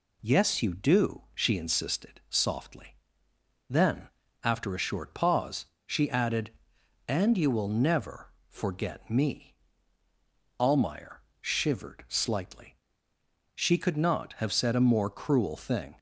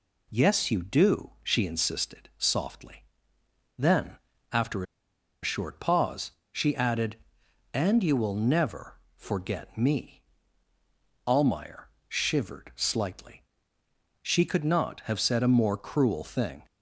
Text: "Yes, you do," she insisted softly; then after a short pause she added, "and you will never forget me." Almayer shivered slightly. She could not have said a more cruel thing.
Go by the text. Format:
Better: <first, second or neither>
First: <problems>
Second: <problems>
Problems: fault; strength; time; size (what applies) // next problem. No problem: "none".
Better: first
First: pauses between "then" and "after"; slight; at 4.0 s; 0.34 s long // pauses between "pause" and "she"; slight; at 5.6 s; 0.20 s long // pauses between "never" and "forget"; slight; at 8.3 s; 0.15 s long // pauses between "Almayer" and "shivered"; slight; at 11.2 s; 0.18 s long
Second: pauses between "then" and "after"; slight; at 4.1 s; 0.34 s long // pauses between "after" and "a"; noticeable; at 4.8 s; 0.58 s long // pauses between "pause" and "she"; slight; at 6.3 s; 0.20 s long // pauses between "never" and "forget"; slight; at 8.9 s; 0.16 s long // pauses between "Almayer" and "shivered"; slight; at 11.8 s; 0.18 s long